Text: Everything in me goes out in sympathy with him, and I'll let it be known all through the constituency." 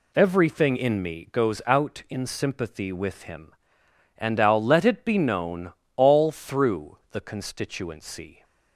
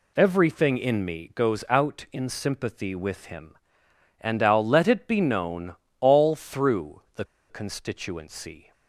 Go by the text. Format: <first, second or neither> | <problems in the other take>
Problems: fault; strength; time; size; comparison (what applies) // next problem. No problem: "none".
first | pauses between "known" and "all"; slight; at 5.7 s; 0.26 s long; slight in the first // pauses between "the" and "constituency"; slight; at 7.2 s; 0.26 s long